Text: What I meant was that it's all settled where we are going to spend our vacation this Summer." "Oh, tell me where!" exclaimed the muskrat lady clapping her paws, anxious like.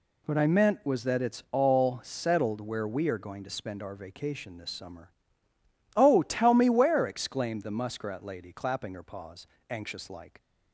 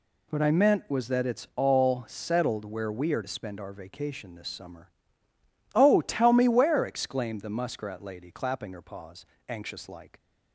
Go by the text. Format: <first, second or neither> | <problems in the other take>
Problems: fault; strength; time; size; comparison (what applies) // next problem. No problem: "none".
first | skips "going"; at 3.2 s